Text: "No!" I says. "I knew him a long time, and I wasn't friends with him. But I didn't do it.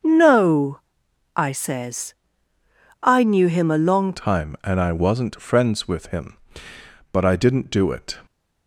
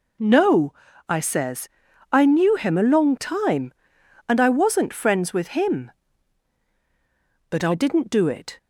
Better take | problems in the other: second | starts louder than the rest; until 1.6 s; 6.5 dB // changes voice at "time"; from 4.1 s on; 4.0 s long

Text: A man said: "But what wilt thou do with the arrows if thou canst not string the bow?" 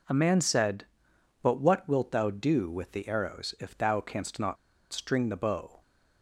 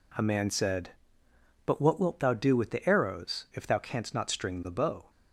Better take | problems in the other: second | pauses between "not" and "string"; slight; at 4.5 s; 0.35 s long

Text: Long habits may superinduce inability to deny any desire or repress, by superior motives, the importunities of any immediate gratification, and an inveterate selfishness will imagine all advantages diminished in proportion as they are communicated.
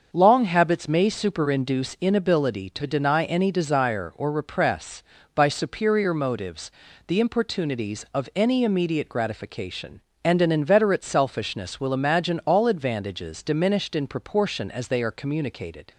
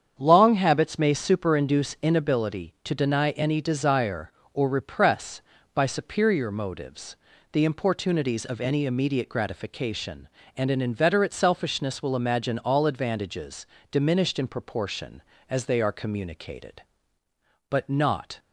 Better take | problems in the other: first | starts louder than the rest; strong; until 1.2 s; 8 dB; also in the first // pauses between "advantages" and "diminished"; slight; at 13.6 s; 0.24 s long // goes on to say "But not"; noticeable; from 17.6 s on; 0.68 s long

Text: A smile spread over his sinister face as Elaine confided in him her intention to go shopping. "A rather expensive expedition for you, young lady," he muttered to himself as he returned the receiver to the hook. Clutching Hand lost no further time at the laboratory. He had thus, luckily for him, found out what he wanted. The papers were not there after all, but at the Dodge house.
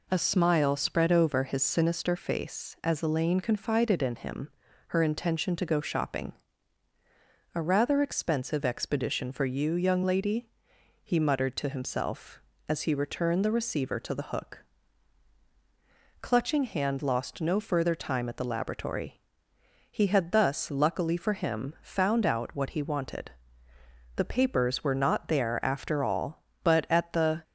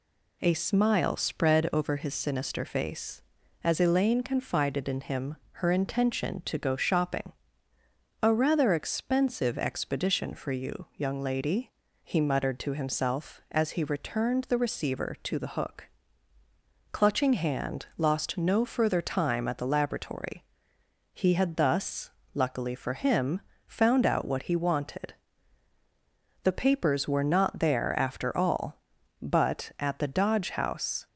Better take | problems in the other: second | pauses between "him" and "her"; at 4.4 s; 0.40 s long; slight in the second // stops before "Dodge house"; at 27.4 s

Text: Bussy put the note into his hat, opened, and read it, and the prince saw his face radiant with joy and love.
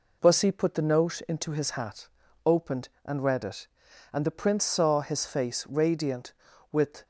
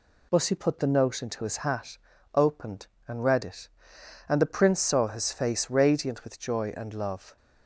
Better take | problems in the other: second | stops before "joy and love"; at 7.0 s

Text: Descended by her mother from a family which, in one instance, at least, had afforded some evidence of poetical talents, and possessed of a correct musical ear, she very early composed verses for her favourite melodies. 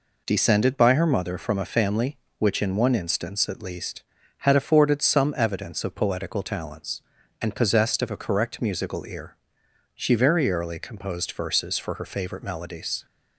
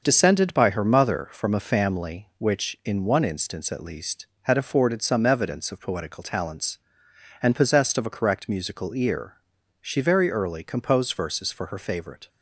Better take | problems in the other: first | starts louder than the rest; until 1.0 s; 6.5 dB // stops before "melodies"; at 12.2 s

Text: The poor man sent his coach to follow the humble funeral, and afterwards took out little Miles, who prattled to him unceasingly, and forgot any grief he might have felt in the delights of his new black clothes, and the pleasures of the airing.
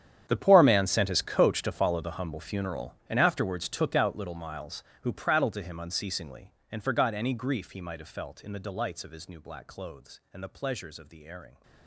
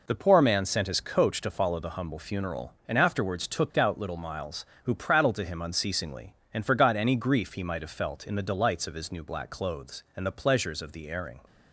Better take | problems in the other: second | gets quieter; strong; throughout; 17.5 dB

